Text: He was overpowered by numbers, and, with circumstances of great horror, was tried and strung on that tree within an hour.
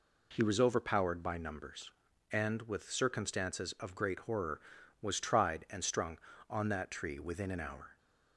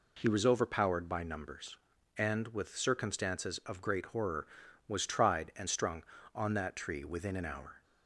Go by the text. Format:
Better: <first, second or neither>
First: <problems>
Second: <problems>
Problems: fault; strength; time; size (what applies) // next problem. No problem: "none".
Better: neither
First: none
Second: none